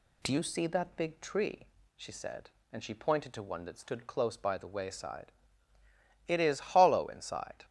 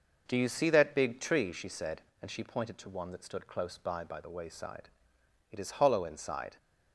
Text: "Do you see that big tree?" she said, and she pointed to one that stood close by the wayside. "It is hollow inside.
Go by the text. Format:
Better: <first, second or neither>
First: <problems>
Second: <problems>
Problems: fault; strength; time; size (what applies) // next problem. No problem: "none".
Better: first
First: none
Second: says "by" twice; at 4.0 s